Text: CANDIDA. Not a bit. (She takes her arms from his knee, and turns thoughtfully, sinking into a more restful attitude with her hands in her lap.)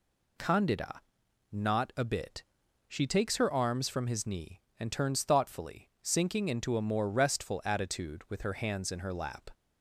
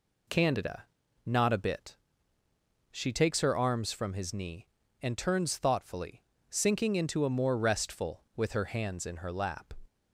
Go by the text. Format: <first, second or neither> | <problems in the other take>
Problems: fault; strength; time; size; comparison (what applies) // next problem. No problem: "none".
first | skips "attitude"; at 8.2 s